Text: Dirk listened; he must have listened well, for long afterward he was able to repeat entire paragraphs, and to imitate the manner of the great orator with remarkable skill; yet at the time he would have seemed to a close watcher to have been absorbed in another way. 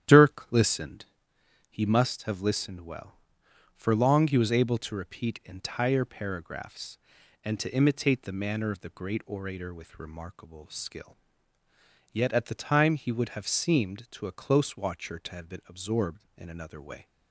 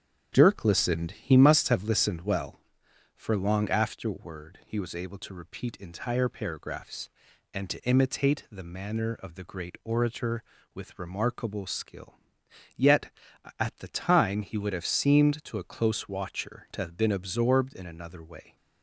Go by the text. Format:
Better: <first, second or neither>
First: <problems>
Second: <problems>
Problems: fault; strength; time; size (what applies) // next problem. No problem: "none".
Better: second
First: starts louder than the rest; strong; until 1.7 s; 10 dB // skips "afterward"; at 4.2 s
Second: starts louder than the rest; strong; until 1.3 s; 8.5 dB